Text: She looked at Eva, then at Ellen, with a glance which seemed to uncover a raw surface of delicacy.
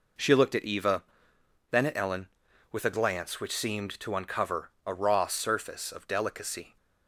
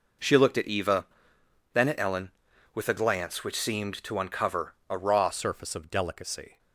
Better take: first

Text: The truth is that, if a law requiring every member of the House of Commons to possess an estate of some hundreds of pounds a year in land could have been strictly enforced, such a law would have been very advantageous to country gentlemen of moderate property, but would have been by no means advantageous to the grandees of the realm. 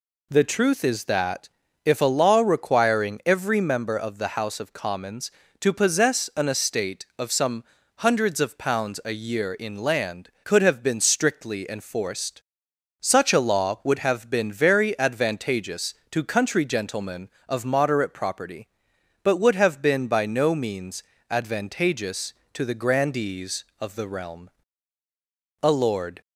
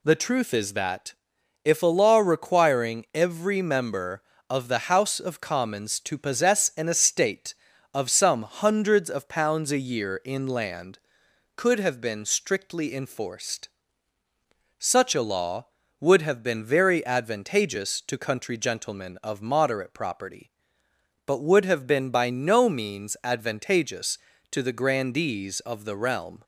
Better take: second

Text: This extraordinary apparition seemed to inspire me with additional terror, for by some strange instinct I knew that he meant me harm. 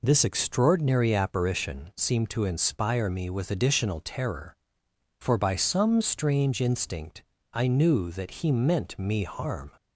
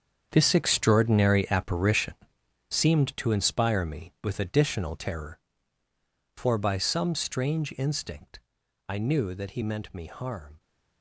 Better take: first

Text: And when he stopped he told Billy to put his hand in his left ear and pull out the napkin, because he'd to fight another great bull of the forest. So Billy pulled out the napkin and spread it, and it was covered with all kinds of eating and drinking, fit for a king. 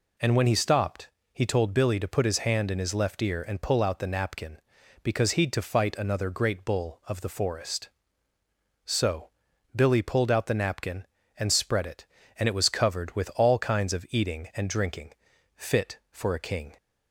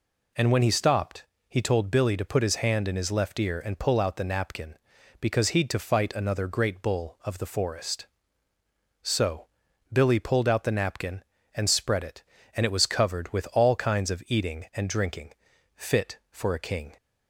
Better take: neither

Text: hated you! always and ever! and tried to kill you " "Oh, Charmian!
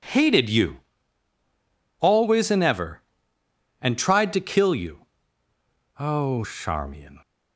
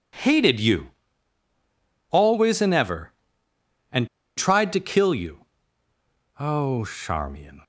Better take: first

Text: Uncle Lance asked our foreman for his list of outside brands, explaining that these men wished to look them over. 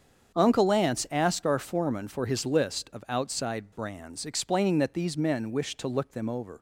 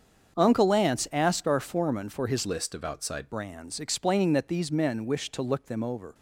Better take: first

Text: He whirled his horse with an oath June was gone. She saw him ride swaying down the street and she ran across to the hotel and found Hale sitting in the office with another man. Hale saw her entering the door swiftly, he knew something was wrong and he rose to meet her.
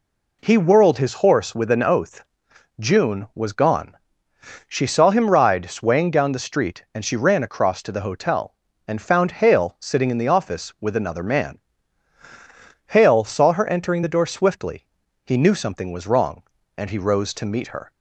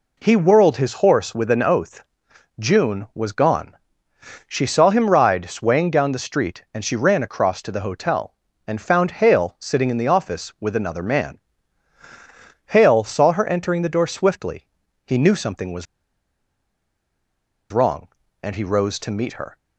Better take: first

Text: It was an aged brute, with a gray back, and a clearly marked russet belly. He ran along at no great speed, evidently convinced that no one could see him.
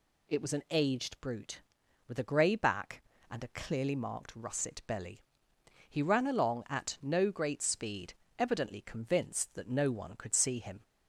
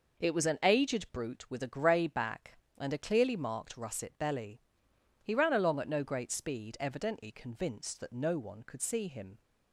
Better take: neither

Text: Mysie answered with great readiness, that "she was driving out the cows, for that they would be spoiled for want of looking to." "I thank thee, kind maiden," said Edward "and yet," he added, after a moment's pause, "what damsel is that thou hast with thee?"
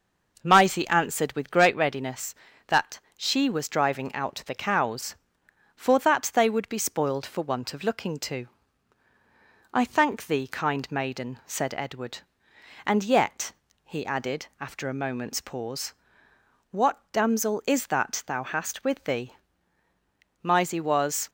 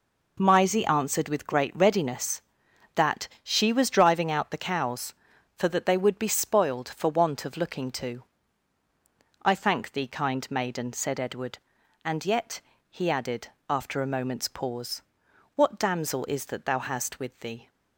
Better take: second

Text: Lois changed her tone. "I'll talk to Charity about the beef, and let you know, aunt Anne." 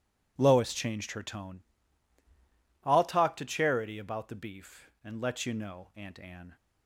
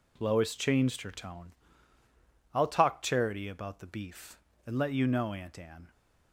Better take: first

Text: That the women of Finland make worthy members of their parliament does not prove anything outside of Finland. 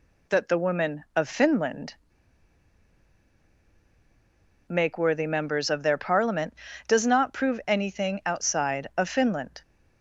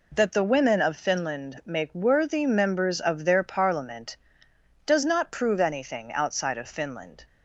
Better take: second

